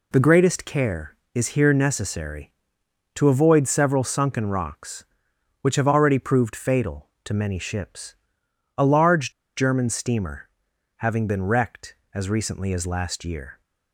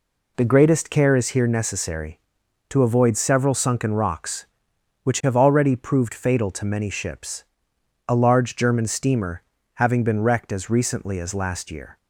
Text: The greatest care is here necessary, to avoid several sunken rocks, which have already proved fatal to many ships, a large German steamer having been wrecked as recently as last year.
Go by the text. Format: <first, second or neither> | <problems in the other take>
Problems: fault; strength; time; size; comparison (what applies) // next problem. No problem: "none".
second | pauses between "large" and "German"; slight; at 9.3 s; 0.25 s long // pauses between "steamer" and "having"; noticeable; at 10.4 s; 0.48 s long; slight in the second